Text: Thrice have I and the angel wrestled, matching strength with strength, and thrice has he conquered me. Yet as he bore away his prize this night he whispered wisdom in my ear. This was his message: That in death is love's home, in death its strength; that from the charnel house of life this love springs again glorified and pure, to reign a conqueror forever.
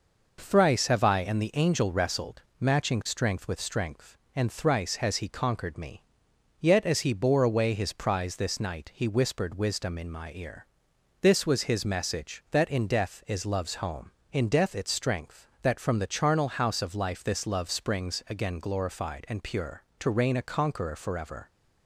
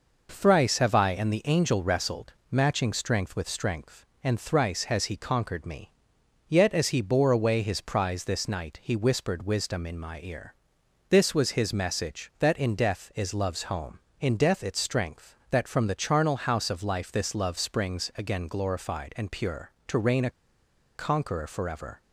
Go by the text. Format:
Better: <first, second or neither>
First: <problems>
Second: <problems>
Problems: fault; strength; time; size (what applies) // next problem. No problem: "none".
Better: first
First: none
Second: pauses between "a" and "conqueror"; noticeable; at 20.3 s; 0.64 s long